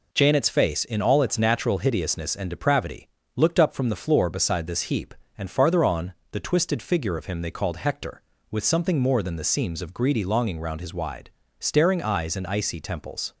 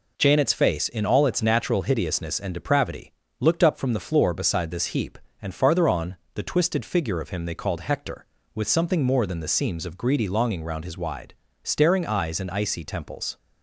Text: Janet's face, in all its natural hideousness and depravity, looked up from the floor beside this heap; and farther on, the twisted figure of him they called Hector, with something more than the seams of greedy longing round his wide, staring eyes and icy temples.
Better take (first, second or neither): neither